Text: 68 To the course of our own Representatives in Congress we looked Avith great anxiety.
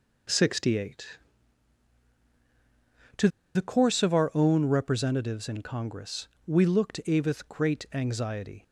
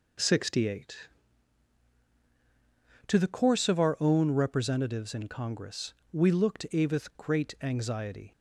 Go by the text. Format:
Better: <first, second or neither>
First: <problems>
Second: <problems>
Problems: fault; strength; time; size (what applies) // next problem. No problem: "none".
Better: second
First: pauses between "To" and "the"; slight; at 3.2 s; 0.26 s long // pauses between "Congress" and "we"; slight; at 6.2 s; 0.18 s long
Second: pauses between "Congress" and "we"; slight; at 5.9 s; 0.18 s long